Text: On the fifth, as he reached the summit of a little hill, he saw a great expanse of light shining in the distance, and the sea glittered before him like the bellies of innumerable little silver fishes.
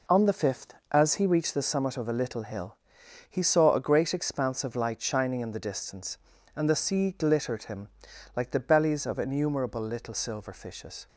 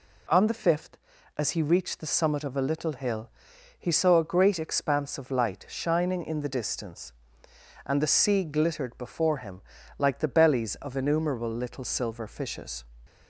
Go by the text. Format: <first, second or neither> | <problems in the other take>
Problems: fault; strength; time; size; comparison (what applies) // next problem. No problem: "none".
second | skips "before"; at 7.6 s // pauses between "him" and "like"; at 7.8 s; 0.44 s long; slight in the second